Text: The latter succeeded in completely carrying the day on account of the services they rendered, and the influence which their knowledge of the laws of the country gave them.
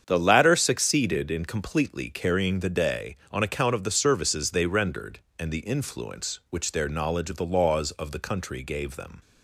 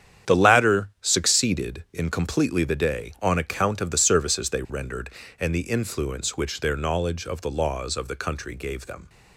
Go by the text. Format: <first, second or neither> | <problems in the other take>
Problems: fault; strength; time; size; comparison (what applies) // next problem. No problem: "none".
first | starts louder than the rest; strong; until 1.4 s; 9 dB; strong in the first // skips "carrying"; at 2.6 s